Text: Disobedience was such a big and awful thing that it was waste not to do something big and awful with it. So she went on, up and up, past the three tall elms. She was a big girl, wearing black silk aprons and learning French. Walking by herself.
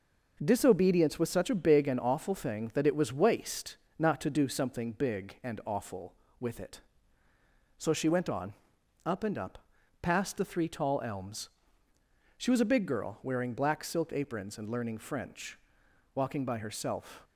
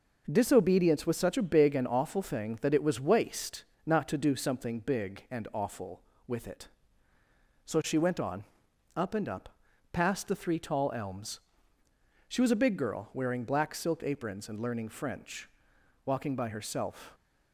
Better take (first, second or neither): neither